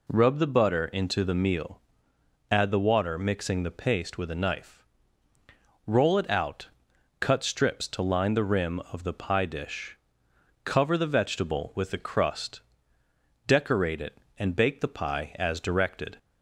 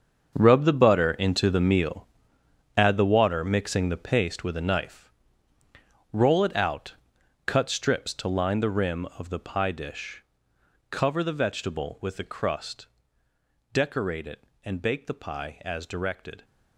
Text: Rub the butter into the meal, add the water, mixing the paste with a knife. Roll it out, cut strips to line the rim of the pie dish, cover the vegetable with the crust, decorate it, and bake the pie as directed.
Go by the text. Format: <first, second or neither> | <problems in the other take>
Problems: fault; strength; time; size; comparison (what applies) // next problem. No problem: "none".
first | gets quieter; strong; throughout; 12.5 dB